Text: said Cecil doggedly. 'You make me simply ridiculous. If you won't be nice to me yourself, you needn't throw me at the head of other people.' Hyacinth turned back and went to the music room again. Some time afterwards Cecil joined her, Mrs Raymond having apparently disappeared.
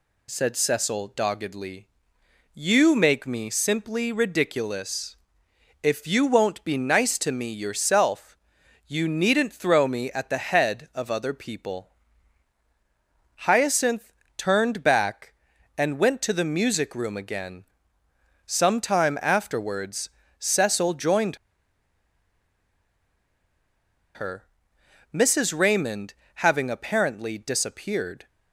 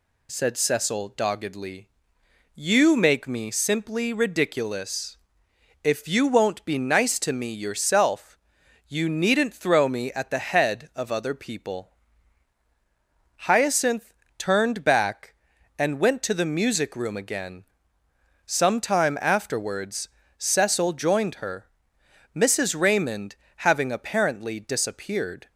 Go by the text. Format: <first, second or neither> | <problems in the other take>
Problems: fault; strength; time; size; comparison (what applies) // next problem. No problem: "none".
second | pauses between "Hyacinth" and "turned"; slight; at 14.1 s; 0.26 s long; slight in the second // pauses between "afterwards" and "Cecil"; slight; at 20.0 s; 0.30 s long; slight in the second // pauses between "joined" and "her"; strong; at 21.3 s; 2.7 s long // pauses between "Raymond" and "having"; slight; at 26.1 s; 0.22 s long; slight in the second